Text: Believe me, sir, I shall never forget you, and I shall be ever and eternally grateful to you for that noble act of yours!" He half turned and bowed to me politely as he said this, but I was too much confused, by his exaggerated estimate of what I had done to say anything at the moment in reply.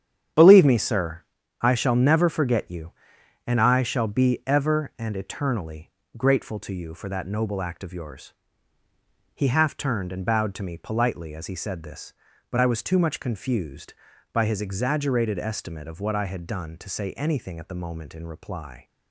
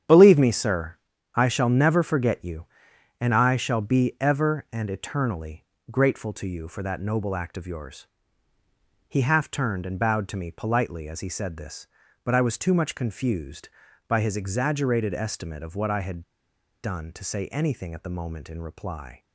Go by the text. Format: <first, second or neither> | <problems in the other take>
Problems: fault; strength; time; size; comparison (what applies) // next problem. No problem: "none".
first | starts louder than the rest; strong; until 1.4 s; 9 dB; strong in the first // pauses between "eternally" and "grateful"; slight; at 5.6 s; 0.26 s long; slight in the first // pauses between "had" and "done"; noticeable; at 16.2 s; 0.61 s long